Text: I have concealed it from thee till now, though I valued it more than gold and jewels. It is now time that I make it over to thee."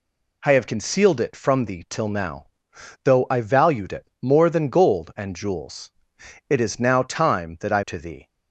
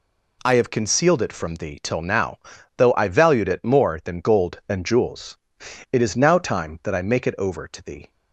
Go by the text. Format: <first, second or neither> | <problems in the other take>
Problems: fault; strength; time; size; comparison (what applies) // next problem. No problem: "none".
second | skips "make it over"; at 7.8 s